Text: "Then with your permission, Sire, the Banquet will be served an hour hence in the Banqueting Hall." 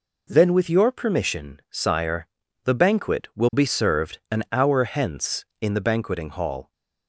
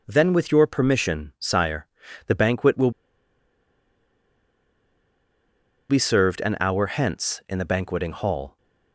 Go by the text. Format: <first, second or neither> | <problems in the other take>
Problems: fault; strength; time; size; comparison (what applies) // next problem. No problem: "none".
first | pauses between "will" and "be"; strong; at 2.9 s; 2.9 s long